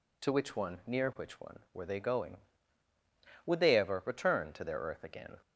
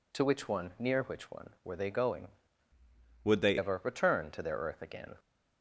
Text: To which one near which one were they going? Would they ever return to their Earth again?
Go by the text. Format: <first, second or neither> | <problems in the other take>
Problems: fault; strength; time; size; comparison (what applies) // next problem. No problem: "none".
first | changes voice from "Would" to "they"; from 3.2 to 3.5 s; 0.3 s long